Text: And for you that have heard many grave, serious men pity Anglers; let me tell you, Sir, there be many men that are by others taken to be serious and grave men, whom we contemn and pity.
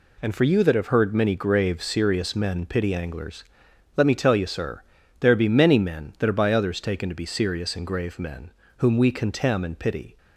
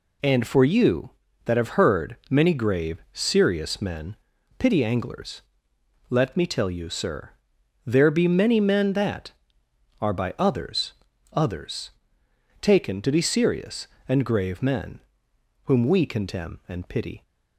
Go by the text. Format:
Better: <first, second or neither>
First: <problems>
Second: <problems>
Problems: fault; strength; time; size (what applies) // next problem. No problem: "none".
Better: first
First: none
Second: pauses between "men" and "pity"; at 4.1 s; 0.42 s long // says "others" twice; at 11.3 s